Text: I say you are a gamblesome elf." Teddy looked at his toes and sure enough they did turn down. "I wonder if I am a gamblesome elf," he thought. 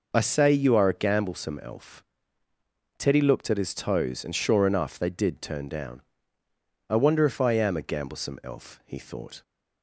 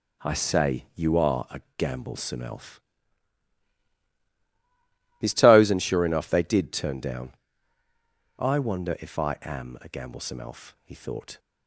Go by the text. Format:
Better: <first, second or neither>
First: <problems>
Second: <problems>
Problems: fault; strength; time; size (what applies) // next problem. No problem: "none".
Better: first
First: none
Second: pauses between "a" and "gamblesome"; slight; at 1.6 s; 0.16 s long // skips "Teddy looked at"; at 4.0 s